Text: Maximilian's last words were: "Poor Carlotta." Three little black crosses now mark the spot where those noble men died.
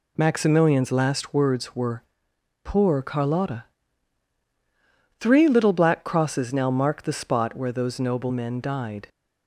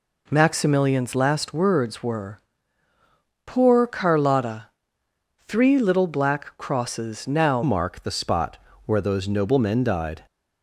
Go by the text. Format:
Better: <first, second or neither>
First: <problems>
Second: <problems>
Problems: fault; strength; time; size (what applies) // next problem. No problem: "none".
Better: first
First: none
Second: changes voice at "mark"; from 7.6 s on; 2.6 s long // pauses between "spot" and "where"; slight; at 8.5 s; 0.28 s long